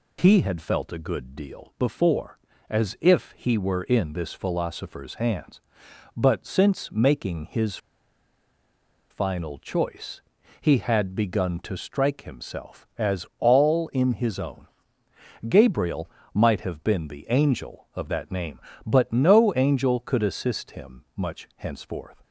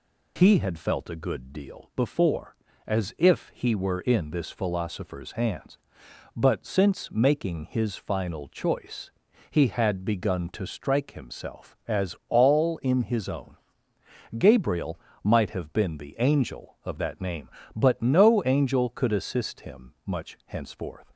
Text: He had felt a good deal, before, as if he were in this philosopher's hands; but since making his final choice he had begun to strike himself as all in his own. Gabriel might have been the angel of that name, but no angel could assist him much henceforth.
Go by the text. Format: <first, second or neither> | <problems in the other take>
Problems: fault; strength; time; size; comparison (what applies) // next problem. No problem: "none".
second | pauses between "his" and "final"; strong; at 7.7 s; 1.3 s long // pauses between "choice" and "he"; at 10.2 s; 0.40 s long; also in the second // pauses between "Gabriel" and "might"; slight; at 16.0 s; 0.28 s long; slight in the second